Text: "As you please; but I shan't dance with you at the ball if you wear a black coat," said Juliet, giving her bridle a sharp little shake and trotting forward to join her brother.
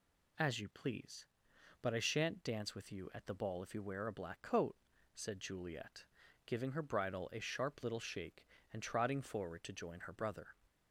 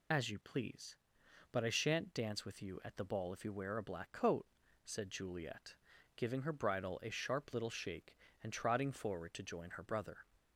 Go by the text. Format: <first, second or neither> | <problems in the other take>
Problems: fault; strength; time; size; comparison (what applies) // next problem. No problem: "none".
first | loses the start of "As"; at 0.1 s; 30 ms